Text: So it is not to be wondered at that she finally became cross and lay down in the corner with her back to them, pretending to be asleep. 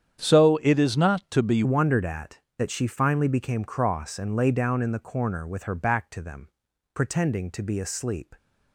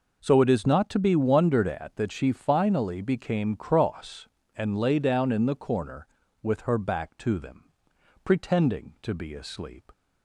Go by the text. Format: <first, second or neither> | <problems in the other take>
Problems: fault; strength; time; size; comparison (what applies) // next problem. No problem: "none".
second | starts louder than the rest; strong; until 1.3 s; 9 dB // changes voice at "wondered"; from 1.6 s on; 6.7 s long